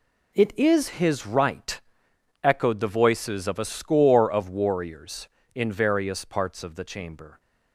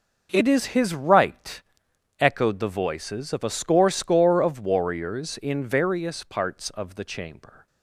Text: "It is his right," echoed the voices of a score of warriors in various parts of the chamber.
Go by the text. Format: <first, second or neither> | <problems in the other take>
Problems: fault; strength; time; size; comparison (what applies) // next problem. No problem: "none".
first | starts louder than the rest; noticeable; until 1.3 s; 6 dB // says "score" twice; at 3.9 s